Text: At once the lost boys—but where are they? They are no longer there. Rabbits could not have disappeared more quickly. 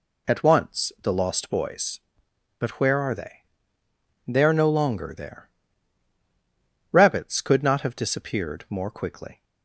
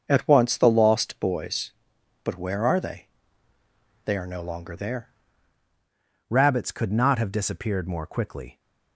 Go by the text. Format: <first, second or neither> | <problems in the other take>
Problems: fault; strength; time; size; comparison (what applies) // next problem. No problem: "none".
first | starts louder than the rest; until 1.1 s; 6.5 dB // changes voice at "Rabbits"; from 6.2 s on; 2.3 s long